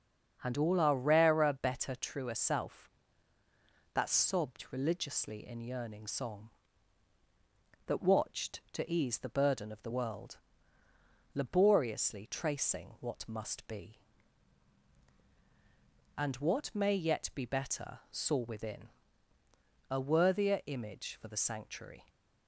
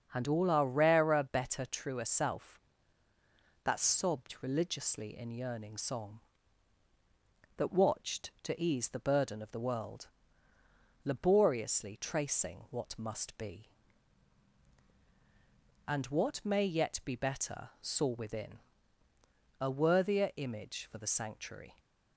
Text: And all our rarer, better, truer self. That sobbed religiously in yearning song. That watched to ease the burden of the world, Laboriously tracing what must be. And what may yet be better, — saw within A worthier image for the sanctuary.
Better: neither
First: starts louder than the rest; until 1.4 s; 7 dB // pauses between "within" and "A"; at 18.8 s; 1.0 s long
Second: starts louder than the rest; until 1.1 s; 7 dB // pauses between "within" and "A"; at 18.5 s; 1.0 s long

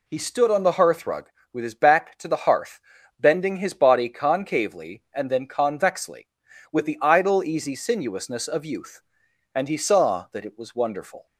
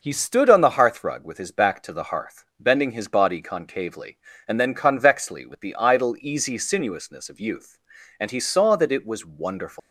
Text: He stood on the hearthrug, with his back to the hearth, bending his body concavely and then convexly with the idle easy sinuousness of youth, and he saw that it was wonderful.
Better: first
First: none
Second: leaves "wonderful" unfinished; at 9.7 s; 130 ms

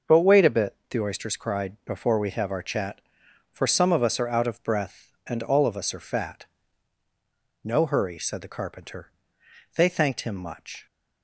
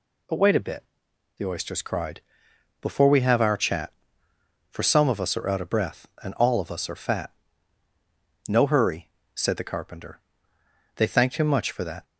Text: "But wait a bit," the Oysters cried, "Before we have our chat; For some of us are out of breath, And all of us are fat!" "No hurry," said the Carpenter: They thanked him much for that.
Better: second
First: starts louder than the rest; noticeable; until 1.2 s; 6 dB // stops before "for that"; at 10.8 s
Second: none

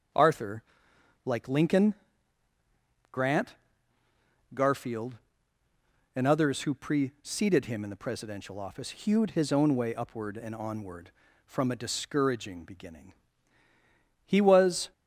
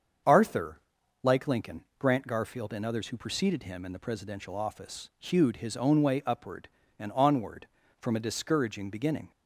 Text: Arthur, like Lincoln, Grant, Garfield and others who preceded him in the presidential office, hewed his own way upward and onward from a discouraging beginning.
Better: second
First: starts louder than the rest; until 1.7 s; 7 dB // goes on to say "He was"; noticeable; from 14.2 s on; 0.66 s long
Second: starts louder than the rest; until 1.7 s; 7 dB

